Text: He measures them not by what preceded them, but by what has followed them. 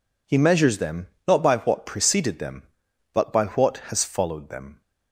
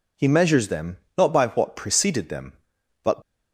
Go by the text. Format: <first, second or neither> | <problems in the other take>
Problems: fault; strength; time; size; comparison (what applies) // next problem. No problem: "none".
first | pauses between "them" and "not"; slight; at 0.9 s; 0.20 s long; slight in the first // stops before "by what has followed them"; at 3.2 s